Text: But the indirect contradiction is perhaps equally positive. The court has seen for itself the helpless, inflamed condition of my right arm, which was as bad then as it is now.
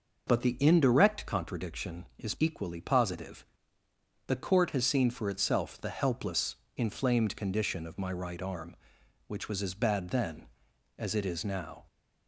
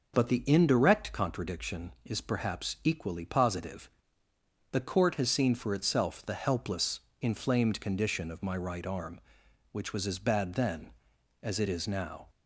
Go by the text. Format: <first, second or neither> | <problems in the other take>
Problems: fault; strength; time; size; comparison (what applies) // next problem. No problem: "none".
second | skips "perhaps"; at 2.3 s